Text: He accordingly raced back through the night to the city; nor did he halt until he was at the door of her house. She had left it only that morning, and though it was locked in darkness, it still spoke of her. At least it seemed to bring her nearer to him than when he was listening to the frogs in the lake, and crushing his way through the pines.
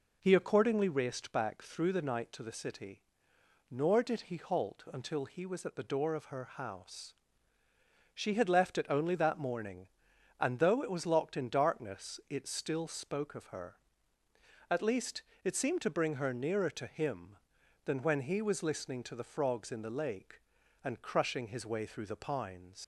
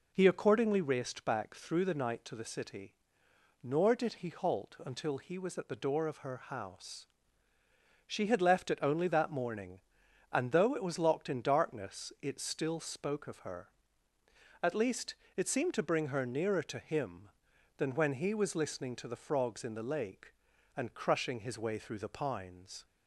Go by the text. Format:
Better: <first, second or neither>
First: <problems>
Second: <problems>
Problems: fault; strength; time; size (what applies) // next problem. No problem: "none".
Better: second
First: pauses between "least" and "it"; slight; at 15.2 s; 0.20 s long // leaves "pines" unfinished; at 22.8 s; 75 ms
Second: pauses between "least" and "it"; slight; at 15.1 s; 0.20 s long